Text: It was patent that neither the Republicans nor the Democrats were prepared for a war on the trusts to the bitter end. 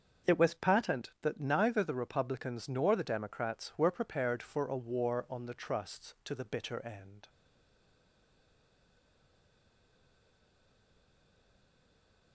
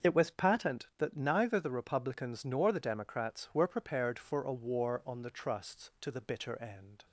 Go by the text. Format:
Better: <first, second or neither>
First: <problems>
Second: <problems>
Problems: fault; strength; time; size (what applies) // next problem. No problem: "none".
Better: second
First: starts louder than the rest; until 1.3 s; 6.5 dB // stays silent after the last word; strong; from 7.2 s on; 5.1 s long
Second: starts louder than the rest; until 1.1 s; 6.5 dB